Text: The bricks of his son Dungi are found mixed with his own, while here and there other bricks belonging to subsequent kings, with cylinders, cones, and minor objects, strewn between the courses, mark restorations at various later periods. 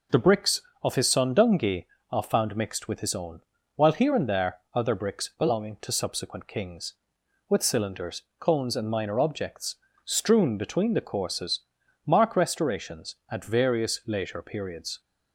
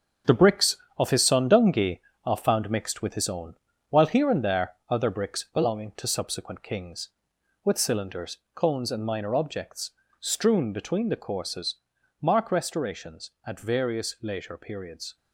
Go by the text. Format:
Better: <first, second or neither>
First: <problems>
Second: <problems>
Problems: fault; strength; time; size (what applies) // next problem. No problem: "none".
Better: first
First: pauses between "there" and "other"; slight; at 4.5 s; 0.16 s long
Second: gets quieter; strong; throughout; 8 dB // pauses between "there" and "other"; slight; at 4.7 s; 0.16 s long